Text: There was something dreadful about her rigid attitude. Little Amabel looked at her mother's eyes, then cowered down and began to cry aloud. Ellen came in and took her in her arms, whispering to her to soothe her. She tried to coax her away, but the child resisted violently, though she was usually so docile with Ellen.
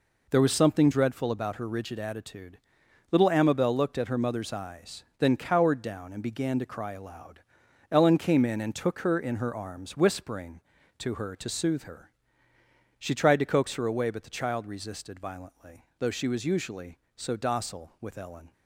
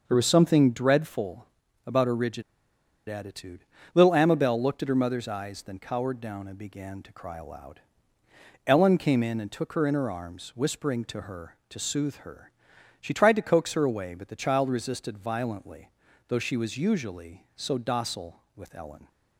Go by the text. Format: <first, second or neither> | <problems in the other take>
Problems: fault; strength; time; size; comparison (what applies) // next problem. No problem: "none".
first | starts louder than the rest; until 1.0 s; 6 dB // pauses between "dreadful" and "about"; at 1.4 s; 0.40 s long // pauses between "rigid" and "attitude"; noticeable; at 2.4 s; 0.67 s long